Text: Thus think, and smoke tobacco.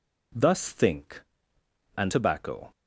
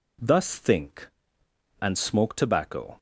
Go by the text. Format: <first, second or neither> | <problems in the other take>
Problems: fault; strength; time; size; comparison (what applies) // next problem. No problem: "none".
second | skips "smoke"; at 2.1 s